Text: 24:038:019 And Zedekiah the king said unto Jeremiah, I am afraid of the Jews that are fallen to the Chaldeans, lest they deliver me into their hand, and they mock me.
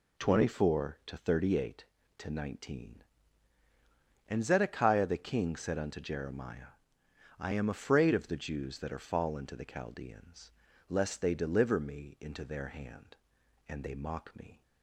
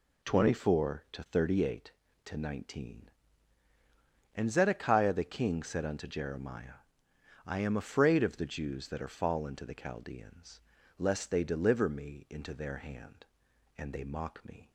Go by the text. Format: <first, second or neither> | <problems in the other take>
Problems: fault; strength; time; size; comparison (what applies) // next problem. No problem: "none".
neither | none